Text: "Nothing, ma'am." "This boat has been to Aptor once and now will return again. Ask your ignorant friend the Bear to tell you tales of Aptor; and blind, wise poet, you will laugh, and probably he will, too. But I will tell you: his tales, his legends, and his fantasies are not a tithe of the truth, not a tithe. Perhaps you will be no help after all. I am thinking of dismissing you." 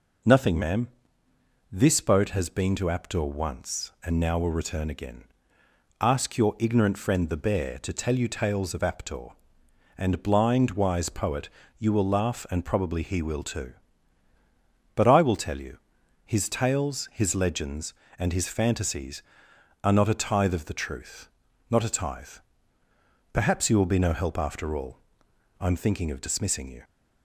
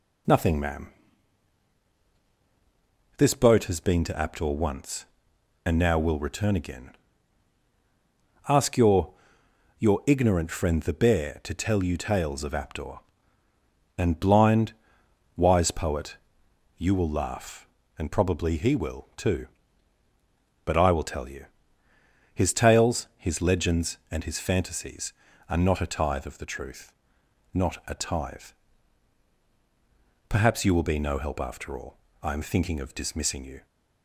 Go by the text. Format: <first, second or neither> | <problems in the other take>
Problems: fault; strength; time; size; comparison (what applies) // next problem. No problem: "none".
first | says "your" twice; at 9.7 s